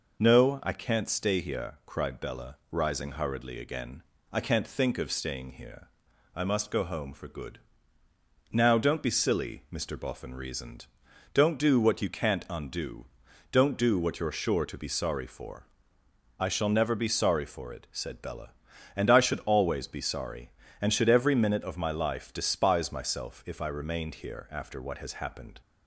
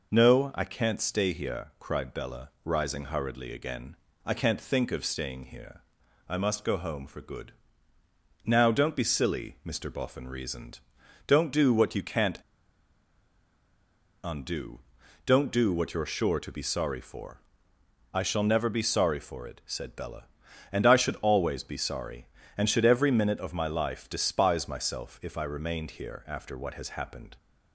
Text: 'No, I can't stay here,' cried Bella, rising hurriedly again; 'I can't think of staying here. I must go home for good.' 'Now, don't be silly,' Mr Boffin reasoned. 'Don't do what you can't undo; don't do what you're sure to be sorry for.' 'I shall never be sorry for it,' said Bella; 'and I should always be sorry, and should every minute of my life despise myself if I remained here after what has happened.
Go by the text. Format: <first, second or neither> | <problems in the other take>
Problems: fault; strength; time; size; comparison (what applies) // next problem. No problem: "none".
first | pauses between "can't" and "undo"; strong; at 12.3 s; 1.8 s long